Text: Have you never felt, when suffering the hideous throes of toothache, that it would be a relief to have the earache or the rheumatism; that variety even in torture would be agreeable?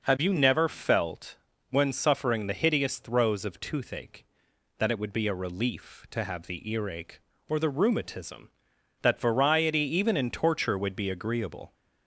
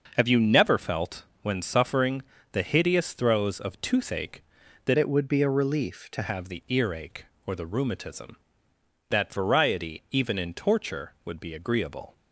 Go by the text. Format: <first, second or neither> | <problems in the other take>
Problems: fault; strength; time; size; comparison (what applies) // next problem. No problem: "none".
first | pauses between "suffering" and "the"; slight; at 2.2 s; 0.30 s long // changes voice from "it" to "to"; from 4.9 to 6.2 s; 1.3 s long